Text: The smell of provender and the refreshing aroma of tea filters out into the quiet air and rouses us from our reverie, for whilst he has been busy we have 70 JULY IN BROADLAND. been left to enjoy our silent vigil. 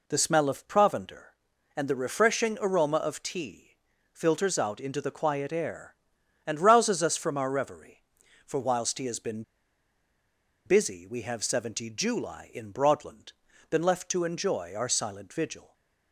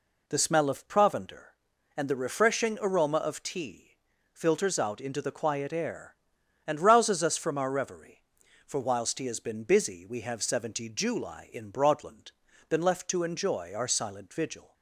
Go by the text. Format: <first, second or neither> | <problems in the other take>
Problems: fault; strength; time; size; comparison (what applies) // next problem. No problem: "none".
second | pauses between "tea" and "filters"; slight; at 3.7 s; 0.34 s long; slight in the second // pauses between "been" and "busy"; at 9.4 s; 1.2 s long